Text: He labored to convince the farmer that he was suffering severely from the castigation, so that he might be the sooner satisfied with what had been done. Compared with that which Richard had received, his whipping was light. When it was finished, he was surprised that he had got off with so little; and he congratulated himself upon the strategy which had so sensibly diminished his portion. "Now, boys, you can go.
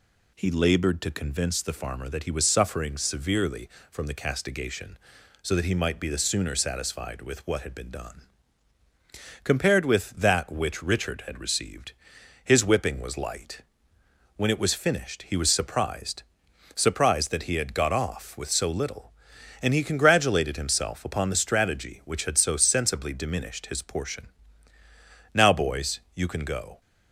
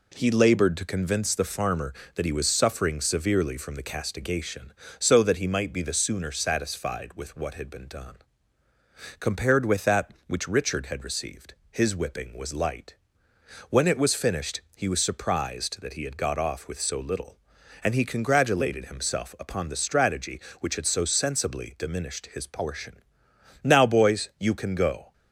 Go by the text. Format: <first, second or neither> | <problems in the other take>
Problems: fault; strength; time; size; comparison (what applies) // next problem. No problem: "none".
second | says "surprised" twice; at 16.7 s